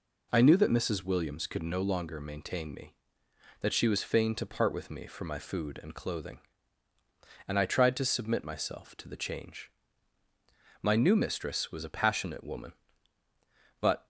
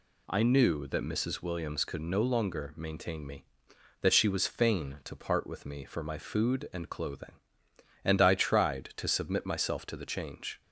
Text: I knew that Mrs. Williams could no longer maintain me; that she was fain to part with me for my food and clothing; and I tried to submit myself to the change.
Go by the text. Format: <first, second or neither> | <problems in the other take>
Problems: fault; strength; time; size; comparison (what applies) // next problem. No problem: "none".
second | goes on to say "My new mistress was a passionate woman but"; strong; from 10.8 s on; 3.2 s long